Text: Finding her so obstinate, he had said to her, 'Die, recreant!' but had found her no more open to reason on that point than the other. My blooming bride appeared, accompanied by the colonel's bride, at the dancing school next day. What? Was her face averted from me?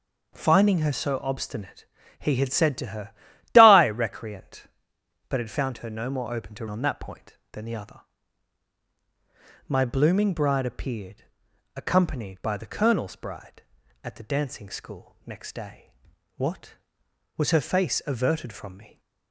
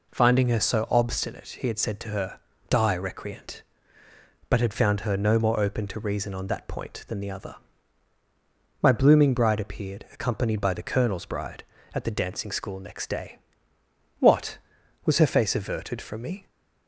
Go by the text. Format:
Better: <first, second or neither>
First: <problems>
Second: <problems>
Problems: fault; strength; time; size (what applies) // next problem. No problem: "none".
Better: second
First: skips "reason"; at 6.6 s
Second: none